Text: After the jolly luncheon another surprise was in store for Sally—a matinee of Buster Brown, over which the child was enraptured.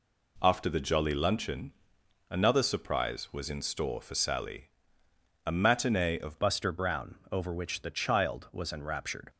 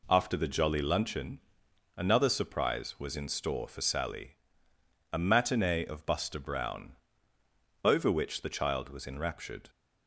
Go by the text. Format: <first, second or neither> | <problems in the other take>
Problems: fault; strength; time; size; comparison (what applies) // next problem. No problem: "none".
second | pauses between "luncheon" and "another"; noticeable; at 1.7 s; 0.56 s long; noticeable in the second // changes voice at "Buster"; from 6.3 s on; 2.9 s long